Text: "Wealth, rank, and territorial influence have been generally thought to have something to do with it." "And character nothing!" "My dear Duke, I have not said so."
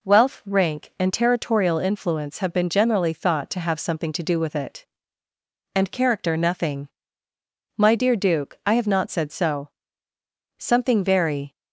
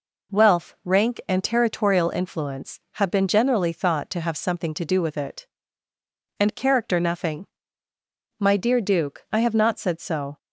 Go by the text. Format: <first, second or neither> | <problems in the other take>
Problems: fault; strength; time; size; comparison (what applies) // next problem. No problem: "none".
second | goes on to say "Something very"; noticeable; from 10.5 s on; 0.98 s long